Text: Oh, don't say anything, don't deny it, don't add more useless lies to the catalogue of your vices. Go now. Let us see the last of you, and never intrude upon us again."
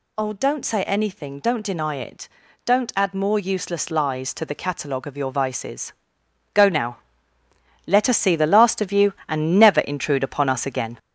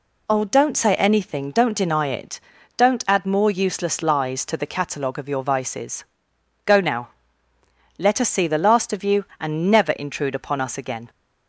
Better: second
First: gets louder; noticeable; throughout; 5.5 dB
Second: none

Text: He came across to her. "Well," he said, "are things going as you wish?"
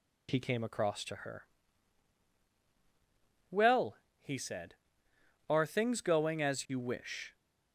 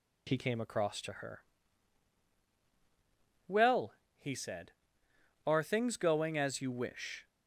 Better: neither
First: none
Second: none

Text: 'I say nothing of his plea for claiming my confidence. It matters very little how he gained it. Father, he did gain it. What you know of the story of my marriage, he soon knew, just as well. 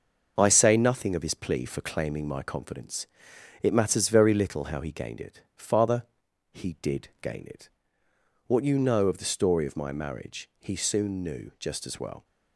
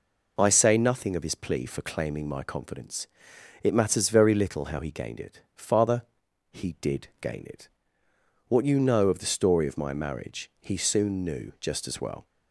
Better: second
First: gets quieter; noticeable; throughout; 6 dB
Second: none

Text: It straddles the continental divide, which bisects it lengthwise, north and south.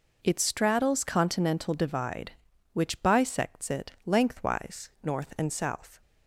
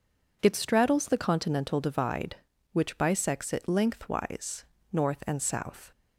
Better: second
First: skips "the"; at 1.0 s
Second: none

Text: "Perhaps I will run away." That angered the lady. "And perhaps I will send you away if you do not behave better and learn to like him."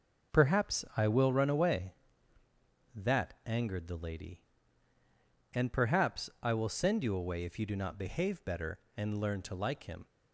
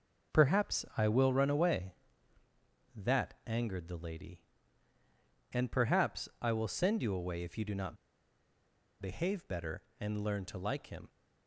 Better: first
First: none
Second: pauses between "not" and "behave"; at 7.9 s; 1.0 s long

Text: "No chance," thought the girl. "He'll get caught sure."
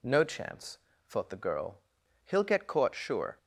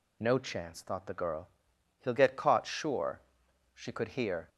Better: first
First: none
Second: goes on to say "She could hear"; noticeable; from 3.7 s on; 0.74 s long

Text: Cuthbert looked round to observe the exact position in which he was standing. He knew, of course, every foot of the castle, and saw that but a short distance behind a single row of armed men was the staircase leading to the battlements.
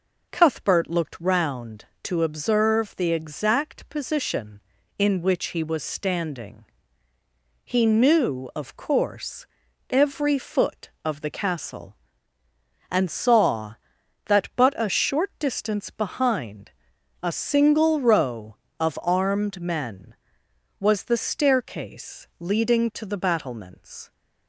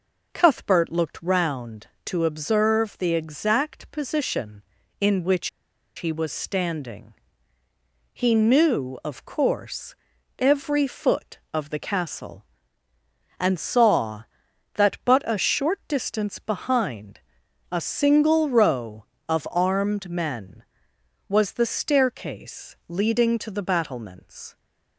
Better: first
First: pauses between "behind" and "a"; noticeable; at 16.7 s; 0.52 s long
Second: pauses between "which" and "he"; noticeable; at 5.4 s; 0.47 s long // pauses between "behind" and "a"; noticeable; at 17.1 s; 0.52 s long

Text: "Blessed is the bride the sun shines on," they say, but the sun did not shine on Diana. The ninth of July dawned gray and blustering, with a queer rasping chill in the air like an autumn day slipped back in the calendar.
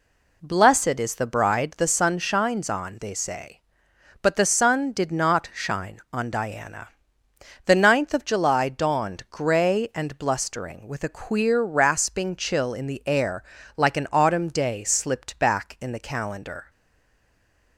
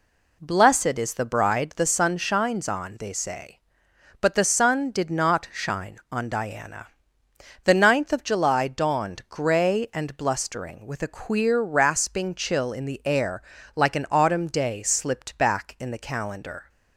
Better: second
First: pauses between "air" and "like"; slight; at 13.4 s; 0.34 s long // stays silent after the last word; from 16.6 s on; 1.1 s long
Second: pauses between "air" and "like"; slight; at 13.4 s; 0.34 s long

